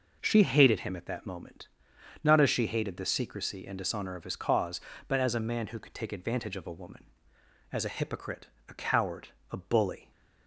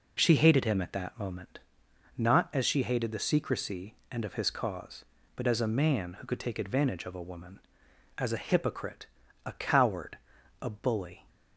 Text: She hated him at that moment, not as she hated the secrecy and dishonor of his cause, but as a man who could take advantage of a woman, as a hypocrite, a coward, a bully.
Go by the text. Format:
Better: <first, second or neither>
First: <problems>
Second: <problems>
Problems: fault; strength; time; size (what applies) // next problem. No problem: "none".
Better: first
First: none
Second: skips "dishonor"; at 4.2 s